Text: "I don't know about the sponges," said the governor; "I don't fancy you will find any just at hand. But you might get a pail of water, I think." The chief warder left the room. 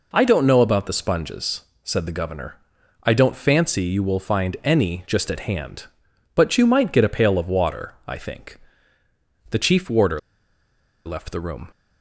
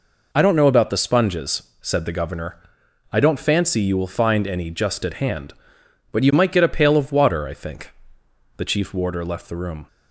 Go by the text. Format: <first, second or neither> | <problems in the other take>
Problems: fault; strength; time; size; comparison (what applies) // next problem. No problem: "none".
second | pauses between "warder" and "left"; noticeable; at 10.1 s; 0.86 s long